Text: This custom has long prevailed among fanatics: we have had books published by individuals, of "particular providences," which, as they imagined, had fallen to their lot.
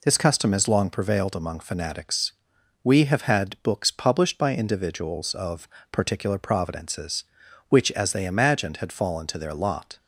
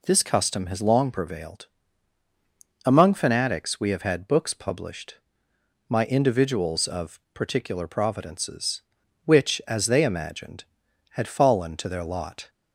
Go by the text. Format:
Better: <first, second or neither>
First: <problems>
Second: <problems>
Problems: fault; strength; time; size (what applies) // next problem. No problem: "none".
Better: first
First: pauses between "of" and "particular"; slight; at 5.6 s; 0.24 s long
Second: pauses between "prevailed" and "among"; at 1.6 s; 1.1 s long // says "my" for "by"; at 5.8 s // pauses between "of" and "particular"; slight; at 7.1 s; 0.16 s long